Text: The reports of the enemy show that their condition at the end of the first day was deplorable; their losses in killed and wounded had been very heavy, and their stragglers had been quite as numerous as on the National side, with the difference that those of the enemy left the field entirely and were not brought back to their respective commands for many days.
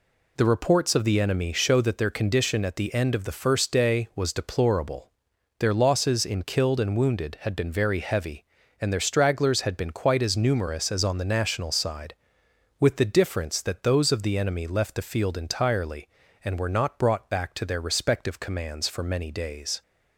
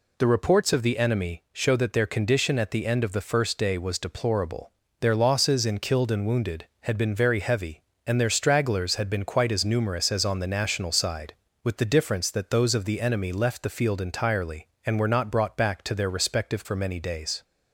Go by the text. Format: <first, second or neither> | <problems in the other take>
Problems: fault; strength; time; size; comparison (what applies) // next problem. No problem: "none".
first | skips "commands"; at 16.6 s